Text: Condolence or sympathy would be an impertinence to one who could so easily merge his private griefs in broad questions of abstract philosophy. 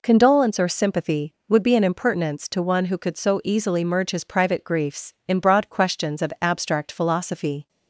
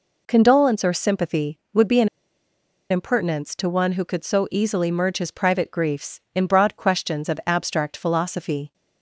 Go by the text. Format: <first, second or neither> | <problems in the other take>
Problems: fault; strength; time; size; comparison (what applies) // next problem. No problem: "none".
first | pauses between "an" and "impertinence"; noticeable; at 2.0 s; 0.82 s long